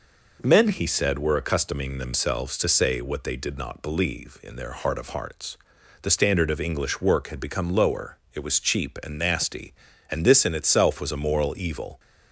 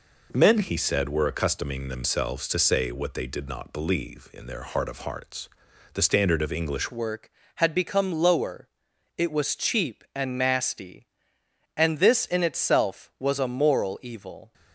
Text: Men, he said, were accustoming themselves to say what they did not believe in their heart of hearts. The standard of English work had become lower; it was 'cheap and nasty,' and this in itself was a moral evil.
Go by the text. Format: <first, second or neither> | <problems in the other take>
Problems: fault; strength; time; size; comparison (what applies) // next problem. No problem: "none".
first | changes voice at "work"; from 6.9 s on; 7.6 s long